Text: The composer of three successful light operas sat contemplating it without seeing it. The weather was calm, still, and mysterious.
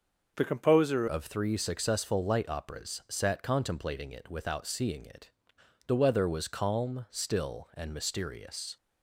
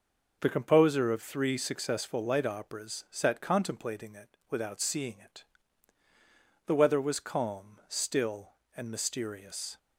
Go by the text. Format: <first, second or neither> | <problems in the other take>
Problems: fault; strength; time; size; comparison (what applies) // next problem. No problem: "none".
second | changes voice at "of"; from 1.0 s on; 7.7 s long